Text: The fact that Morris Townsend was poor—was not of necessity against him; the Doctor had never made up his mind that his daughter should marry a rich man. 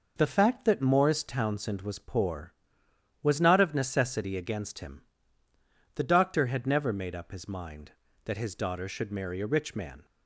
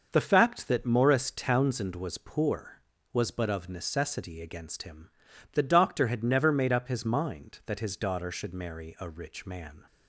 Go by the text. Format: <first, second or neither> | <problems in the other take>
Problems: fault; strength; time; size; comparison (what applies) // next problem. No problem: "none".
first | says "but" for "not"; at 3.2 s